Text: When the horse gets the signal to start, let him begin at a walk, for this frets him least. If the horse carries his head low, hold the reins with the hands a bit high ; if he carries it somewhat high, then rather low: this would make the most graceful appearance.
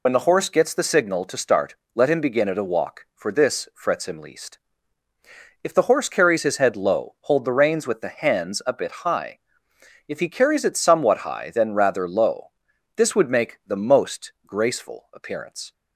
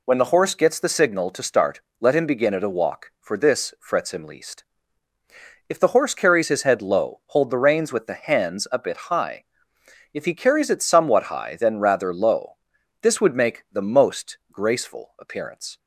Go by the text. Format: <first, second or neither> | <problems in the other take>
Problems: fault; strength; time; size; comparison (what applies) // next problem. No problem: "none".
second | loses the start of "When"; at 0.0 s; 50 ms // pauses between "most" and "graceful"; slight; at 14.3 s; 0.16 s long; slight in the second